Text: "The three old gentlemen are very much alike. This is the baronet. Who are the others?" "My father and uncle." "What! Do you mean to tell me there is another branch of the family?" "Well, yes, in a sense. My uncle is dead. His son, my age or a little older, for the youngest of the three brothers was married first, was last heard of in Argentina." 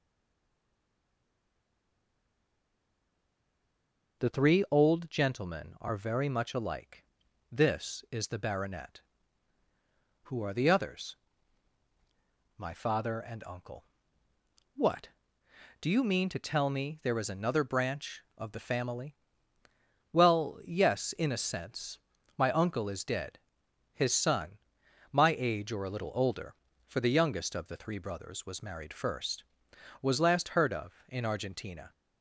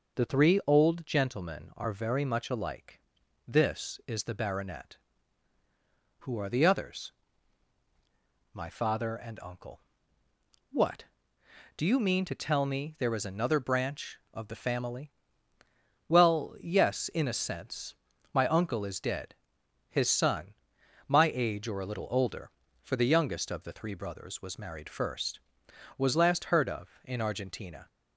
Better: second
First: stays silent before the first word; strong; until 4.1 s; 4.1 s long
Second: none

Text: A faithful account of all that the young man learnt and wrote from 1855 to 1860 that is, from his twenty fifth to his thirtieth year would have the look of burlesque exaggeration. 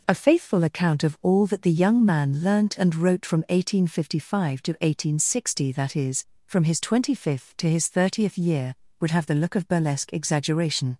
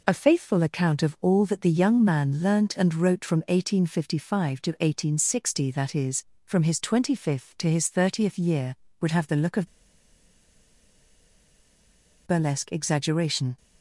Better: first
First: none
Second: pauses between "of" and "burlesque"; strong; at 9.6 s; 2.5 s long

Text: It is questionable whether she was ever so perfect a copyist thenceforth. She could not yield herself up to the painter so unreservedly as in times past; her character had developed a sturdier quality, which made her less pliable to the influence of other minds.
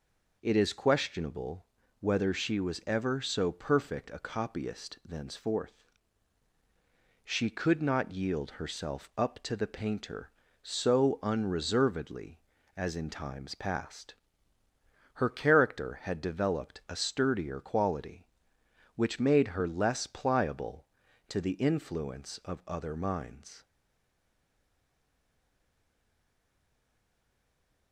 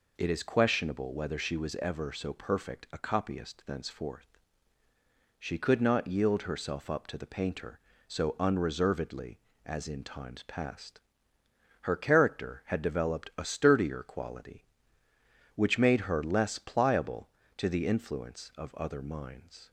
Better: second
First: pauses between "questionable" and "whether"; slight; at 1.6 s; 0.34 s long // stays silent after the last word; strong; from 23.6 s on; 4.3 s long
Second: none

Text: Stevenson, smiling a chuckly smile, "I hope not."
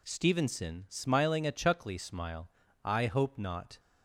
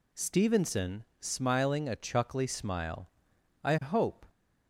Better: first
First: none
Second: stops before "not"; at 4.2 s

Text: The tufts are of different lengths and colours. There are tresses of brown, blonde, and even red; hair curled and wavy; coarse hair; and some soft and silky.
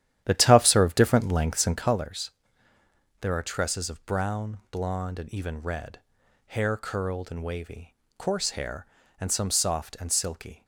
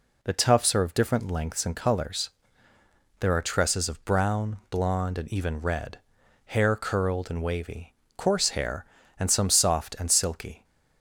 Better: second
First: starts louder than the rest; strong; until 2.1 s; 11 dB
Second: none

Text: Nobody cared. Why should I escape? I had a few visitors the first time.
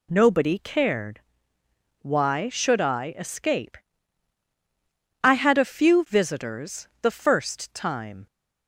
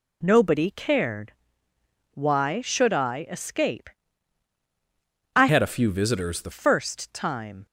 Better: first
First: none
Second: changes voice from "had" to "the"; from 5.4 to 6.5 s; 1.1 s long

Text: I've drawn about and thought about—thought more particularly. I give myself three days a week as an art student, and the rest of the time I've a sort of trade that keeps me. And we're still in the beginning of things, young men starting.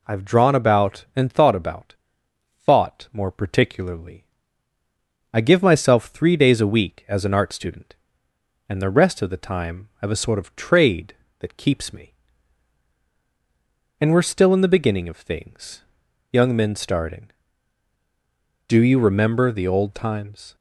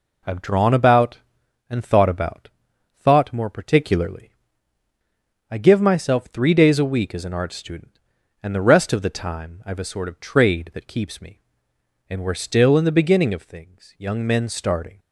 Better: second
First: goes on to say "Do you remember the old times"; strong; from 18.6 s on; 1.8 s long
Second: none

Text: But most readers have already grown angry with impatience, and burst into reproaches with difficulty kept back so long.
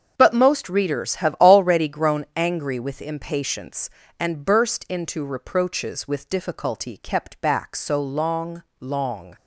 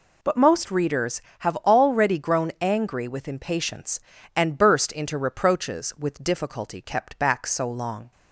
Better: second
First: starts louder than the rest; until 1.1 s; 7 dB // says "long" twice; at 8.7 s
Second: none

